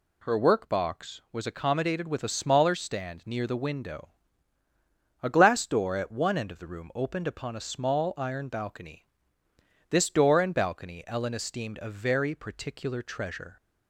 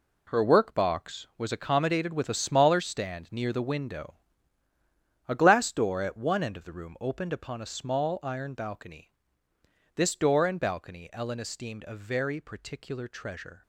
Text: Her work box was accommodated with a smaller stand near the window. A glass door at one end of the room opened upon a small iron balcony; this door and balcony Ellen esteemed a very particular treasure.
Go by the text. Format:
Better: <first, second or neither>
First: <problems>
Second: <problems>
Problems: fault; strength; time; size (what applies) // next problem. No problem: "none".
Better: first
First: none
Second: gets quieter; strong; throughout; 10 dB